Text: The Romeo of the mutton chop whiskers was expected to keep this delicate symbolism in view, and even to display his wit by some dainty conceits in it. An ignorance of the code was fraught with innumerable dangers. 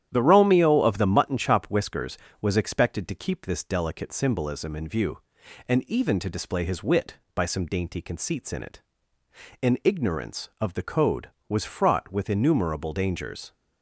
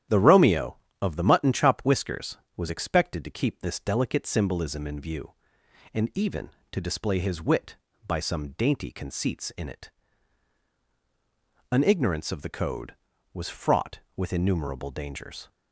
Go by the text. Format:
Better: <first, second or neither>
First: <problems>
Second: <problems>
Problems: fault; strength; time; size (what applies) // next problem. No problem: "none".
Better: neither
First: starts louder than the rest; strong; until 1.1 s; 10.5 dB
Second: starts louder than the rest; strong; until 1.3 s; 11 dB